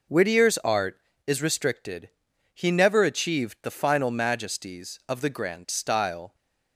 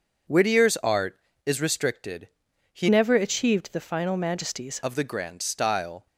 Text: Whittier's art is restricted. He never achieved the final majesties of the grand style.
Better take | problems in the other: first | changes voice from "never" to "majesties"; from 2.8 to 4.7 s; 1.9 s long

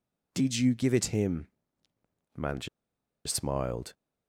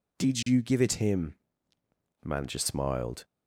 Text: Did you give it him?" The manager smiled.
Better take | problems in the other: second | pauses between "manager" and "smiled"; noticeable; at 2.6 s; 0.58 s long

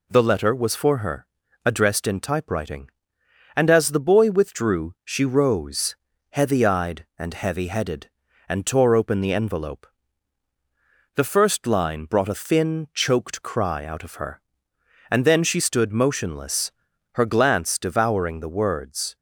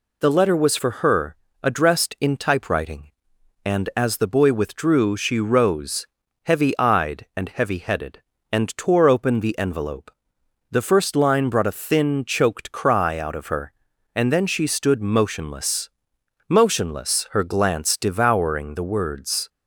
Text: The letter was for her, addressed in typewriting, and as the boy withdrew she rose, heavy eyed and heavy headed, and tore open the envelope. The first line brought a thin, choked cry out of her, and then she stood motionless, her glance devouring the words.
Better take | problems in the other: first | says "motionless" twice; at 16.4 s

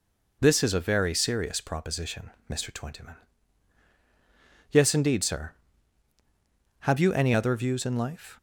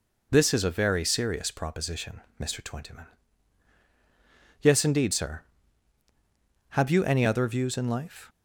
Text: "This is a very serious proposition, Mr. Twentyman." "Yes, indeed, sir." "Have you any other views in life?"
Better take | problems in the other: neither | none

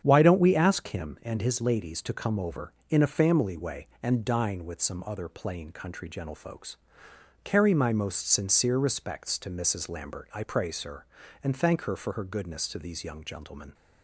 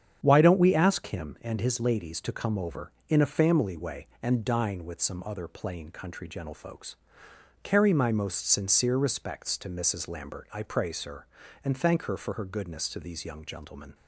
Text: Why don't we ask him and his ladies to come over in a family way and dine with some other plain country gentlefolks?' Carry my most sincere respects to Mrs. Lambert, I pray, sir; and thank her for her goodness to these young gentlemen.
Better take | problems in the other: neither | starts louder than the rest; strong; the same in both

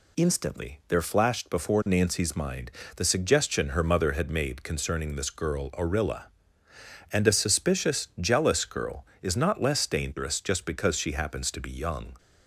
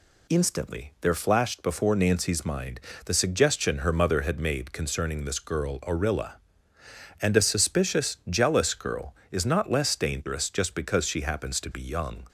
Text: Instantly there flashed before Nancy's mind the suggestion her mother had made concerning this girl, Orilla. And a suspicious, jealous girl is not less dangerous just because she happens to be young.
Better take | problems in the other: neither | pauses between "mind" and "the"; slight; the same in both

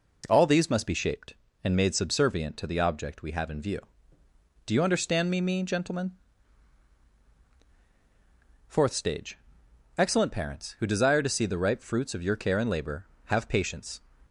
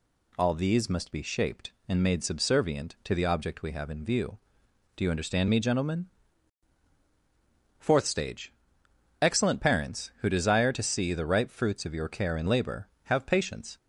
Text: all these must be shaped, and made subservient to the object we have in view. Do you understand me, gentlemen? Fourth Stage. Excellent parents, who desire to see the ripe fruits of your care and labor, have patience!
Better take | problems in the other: second | says "me" twice; at 5.4 s

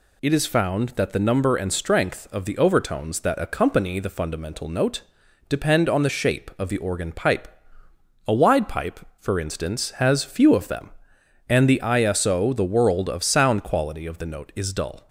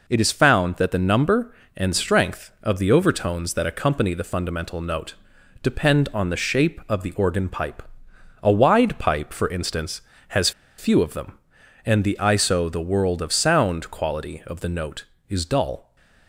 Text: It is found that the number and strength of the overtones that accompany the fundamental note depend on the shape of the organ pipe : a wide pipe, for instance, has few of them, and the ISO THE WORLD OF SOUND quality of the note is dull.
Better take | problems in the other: first | pauses between "note" and "depend"; noticeable; at 5.1 s; 0.48 s long; noticeable in the first // pauses between "has" and "few"; slight; at 10.5 s; 0.27 s long

